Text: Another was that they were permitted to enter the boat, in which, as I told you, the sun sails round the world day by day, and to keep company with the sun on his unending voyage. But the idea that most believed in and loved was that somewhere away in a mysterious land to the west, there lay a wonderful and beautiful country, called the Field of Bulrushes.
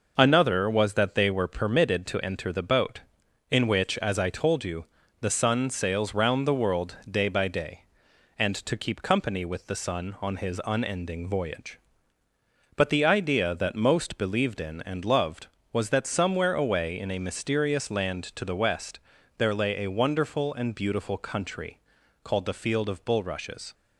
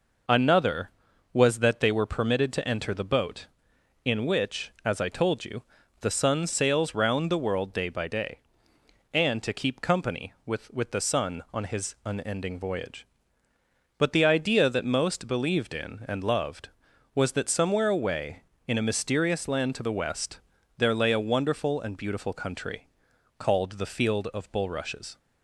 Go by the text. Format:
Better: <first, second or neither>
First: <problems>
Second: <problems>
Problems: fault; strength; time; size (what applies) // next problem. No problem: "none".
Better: first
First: none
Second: says "with" twice; at 10.7 s